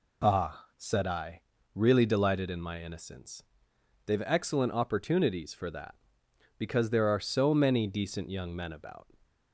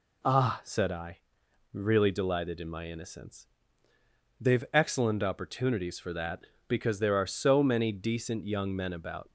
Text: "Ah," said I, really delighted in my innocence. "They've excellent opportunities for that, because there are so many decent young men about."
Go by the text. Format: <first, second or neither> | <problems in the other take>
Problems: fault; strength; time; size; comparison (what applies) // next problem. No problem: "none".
neither | none